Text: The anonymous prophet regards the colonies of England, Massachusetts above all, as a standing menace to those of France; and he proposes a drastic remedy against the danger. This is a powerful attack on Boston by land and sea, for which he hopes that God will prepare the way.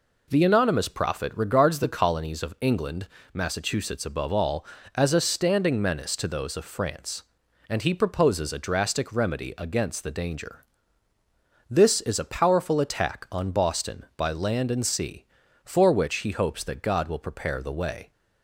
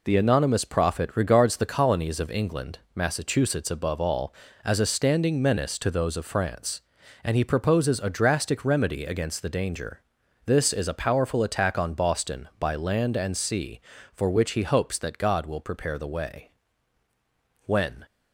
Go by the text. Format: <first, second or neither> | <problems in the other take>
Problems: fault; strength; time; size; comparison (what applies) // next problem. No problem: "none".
first | goes on to say "When"; slight; from 17.6 s on; 0.42 s long